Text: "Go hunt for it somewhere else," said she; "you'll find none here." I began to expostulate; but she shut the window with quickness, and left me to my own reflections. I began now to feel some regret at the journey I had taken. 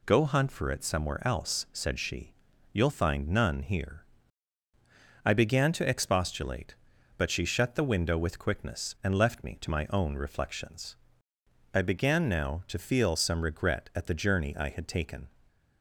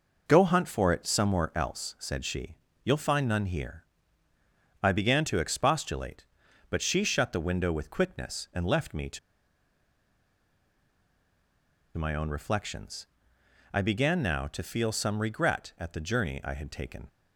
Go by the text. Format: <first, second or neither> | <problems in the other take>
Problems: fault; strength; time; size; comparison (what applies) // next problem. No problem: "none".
first | pauses between "to" and "my"; strong; at 9.1 s; 2.7 s long